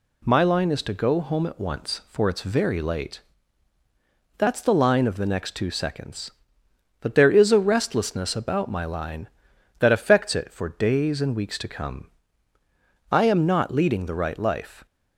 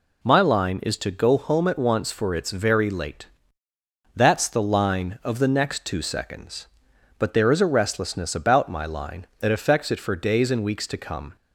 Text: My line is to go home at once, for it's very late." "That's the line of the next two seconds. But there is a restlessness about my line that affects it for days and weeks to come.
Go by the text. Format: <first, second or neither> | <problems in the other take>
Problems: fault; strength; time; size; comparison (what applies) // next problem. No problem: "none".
second | goes on to say "I am not leading the right life"; strong; from 13.1 s on; 1.7 s long